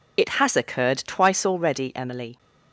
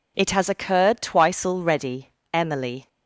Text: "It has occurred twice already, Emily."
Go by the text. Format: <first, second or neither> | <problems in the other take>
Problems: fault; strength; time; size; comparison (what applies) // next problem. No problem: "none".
second | loses the start of "It"; at 0.1 s; 45 ms